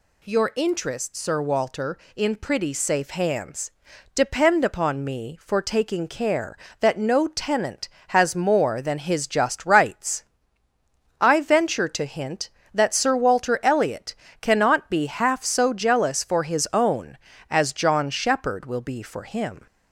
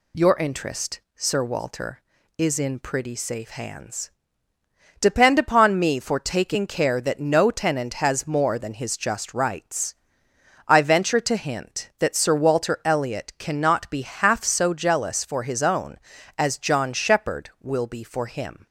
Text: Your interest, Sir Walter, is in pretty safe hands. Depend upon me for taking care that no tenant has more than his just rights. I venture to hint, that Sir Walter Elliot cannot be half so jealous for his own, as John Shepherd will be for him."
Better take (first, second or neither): second